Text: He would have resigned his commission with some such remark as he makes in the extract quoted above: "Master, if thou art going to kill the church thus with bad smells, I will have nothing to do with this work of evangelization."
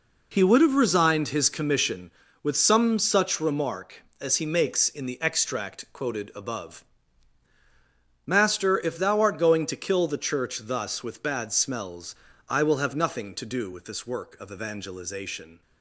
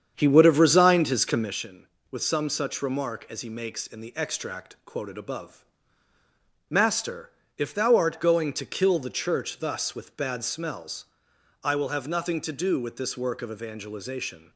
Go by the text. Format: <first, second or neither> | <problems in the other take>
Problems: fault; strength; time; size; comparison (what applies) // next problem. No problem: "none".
first | starts louder than the rest; strong; until 1.6 s; 8 dB